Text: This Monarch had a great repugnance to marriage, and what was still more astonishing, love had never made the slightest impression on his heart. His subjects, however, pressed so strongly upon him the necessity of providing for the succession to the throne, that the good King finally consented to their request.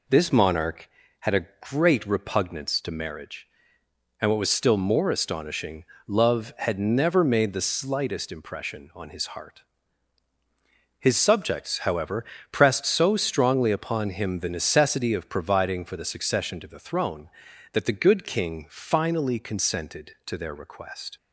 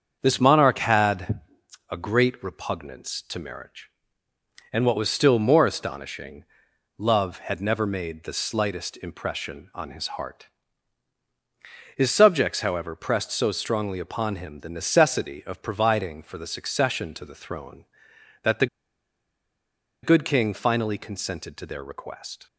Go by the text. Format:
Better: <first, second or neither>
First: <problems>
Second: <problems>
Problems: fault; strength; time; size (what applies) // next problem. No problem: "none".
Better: first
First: none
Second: starts louder than the rest; strong; until 1.2 s; 7 dB // pauses between "had" and "a"; noticeable; at 1.3 s; 0.52 s long // pauses between "the" and "good"; strong; at 18.6 s; 1.3 s long